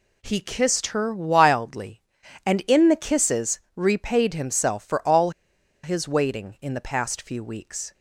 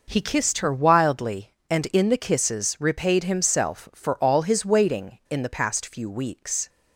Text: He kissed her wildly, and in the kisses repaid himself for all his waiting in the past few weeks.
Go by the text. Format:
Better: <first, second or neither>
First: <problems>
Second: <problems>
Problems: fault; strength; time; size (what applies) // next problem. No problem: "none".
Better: second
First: pauses between "all" and "his"; noticeable; at 5.3 s; 0.53 s long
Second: none